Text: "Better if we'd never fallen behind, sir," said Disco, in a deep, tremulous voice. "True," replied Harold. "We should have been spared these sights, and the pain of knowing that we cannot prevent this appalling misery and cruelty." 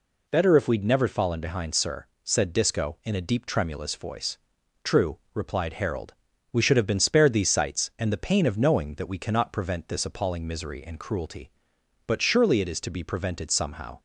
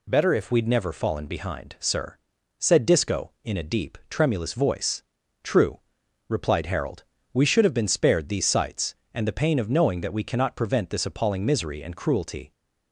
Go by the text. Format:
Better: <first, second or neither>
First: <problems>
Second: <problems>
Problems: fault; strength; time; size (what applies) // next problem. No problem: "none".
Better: second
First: goes on to say "But surely it is to be prevented somehow"; strong; from 12.0 s on; 1.9 s long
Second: none